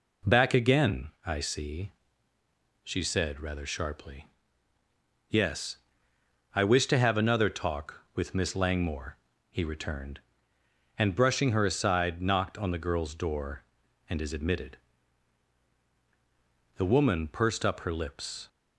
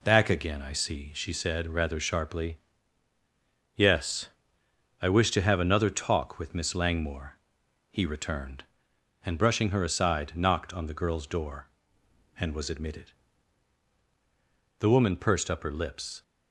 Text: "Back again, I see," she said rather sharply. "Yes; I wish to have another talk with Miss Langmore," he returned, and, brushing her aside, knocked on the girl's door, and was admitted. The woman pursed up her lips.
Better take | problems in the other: second | says "is" for "was"; at 14.2 s

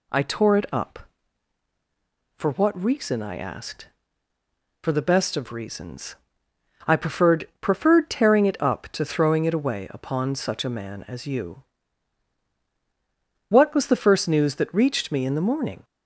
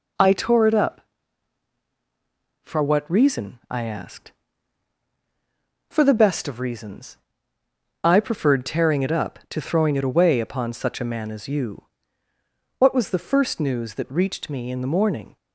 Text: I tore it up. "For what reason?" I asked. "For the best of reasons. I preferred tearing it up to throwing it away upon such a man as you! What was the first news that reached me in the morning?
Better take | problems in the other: second | says "preferred" twice; at 7.6 s

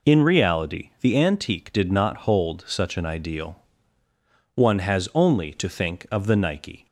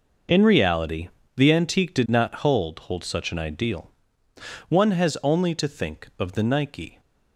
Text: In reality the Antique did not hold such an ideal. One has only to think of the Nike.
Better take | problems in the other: first | pauses between "reality" and "the"; slight; at 1.0 s; 0.30 s long // says "hold" twice; at 2.7 s

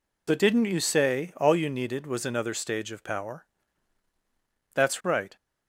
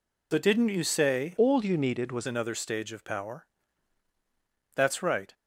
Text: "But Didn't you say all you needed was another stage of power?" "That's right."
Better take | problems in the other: first | changes voice from "all" to "was"; from 1.3 to 2.2 s; 0.9 s long

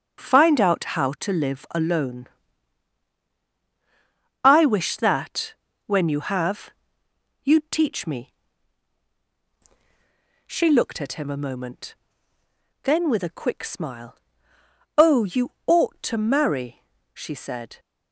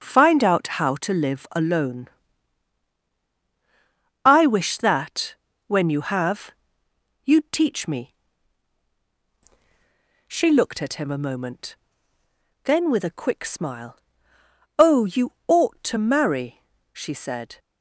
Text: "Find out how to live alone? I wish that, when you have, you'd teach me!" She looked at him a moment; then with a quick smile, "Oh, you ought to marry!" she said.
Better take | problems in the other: neither | pauses between "you" and "ought"; slight; the same in both

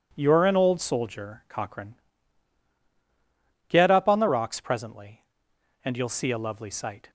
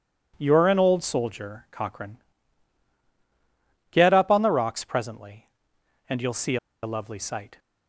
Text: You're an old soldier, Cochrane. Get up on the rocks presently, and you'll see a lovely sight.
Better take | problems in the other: first | pauses between "see" and "a"; slight; at 6.5 s; 0.26 s long

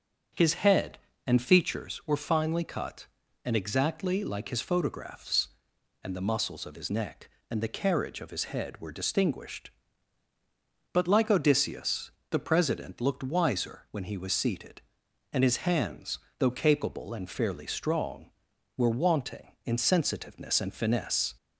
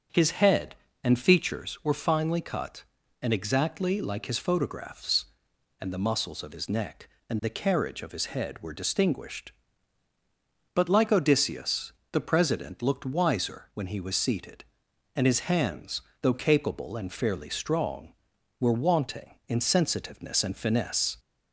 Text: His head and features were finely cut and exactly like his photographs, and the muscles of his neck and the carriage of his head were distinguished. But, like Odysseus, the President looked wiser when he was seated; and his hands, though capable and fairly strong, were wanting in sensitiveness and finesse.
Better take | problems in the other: neither | starts louder than the rest; the same in both

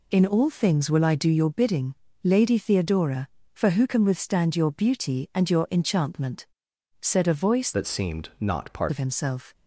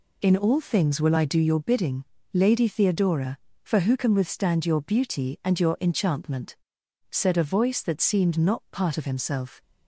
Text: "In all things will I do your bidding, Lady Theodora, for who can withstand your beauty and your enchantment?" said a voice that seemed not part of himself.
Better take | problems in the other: second | changes voice from "that" to "part"; from 7.7 to 8.9 s; 1.2 s long

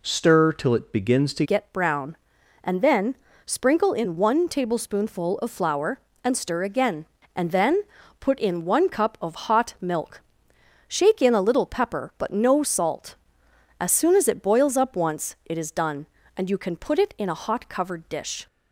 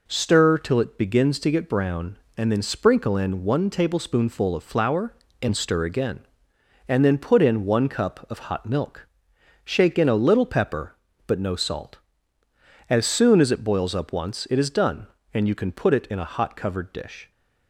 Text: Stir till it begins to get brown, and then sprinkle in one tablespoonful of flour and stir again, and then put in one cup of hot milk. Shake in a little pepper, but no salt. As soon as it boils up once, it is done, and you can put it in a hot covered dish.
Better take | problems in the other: second | changes voice at "get"; from 1.4 s on; 17.0 s long // pauses between "then" and "sprinkle"; slight; at 3.1 s; 0.28 s long // pauses between "then" and "put"; at 7.8 s; 0.38 s long

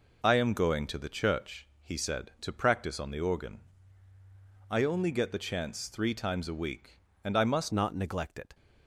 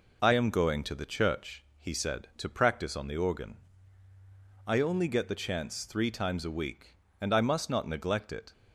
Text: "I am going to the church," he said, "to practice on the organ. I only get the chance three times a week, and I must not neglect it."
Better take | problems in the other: second | changes voice at "not"; from 7.7 s on; 0.8 s long

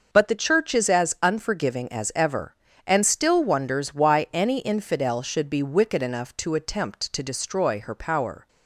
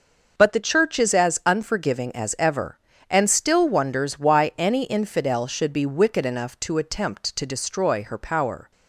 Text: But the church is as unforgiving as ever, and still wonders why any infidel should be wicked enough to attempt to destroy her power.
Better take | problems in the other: neither | none

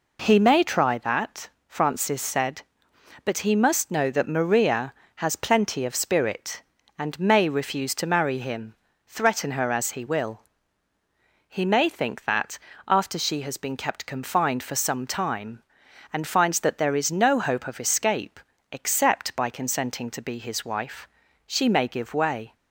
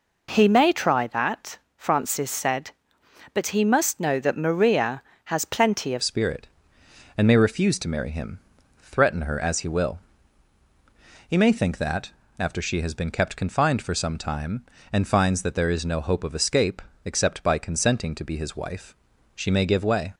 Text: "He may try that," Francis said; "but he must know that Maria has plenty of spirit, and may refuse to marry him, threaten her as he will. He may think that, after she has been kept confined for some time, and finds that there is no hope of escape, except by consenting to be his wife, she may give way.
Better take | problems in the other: first | changes voice at "spirit"; from 6.0 s on; 14.1 s long

